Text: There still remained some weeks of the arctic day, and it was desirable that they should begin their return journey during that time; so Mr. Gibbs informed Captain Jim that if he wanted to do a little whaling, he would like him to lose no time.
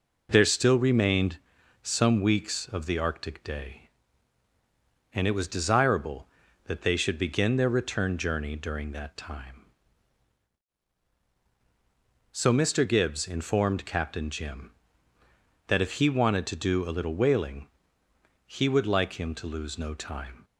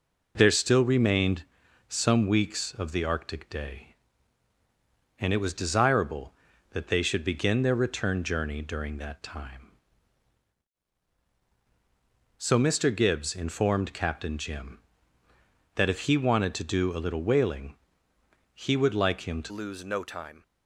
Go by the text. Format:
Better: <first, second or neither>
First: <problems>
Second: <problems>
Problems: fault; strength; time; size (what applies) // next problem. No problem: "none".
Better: first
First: pauses between "remained" and "some"; at 1.3 s; 0.44 s long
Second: pauses between "remained" and "some"; at 1.4 s; 0.44 s long // changes voice at "lose"; from 19.4 s on; 1.0 s long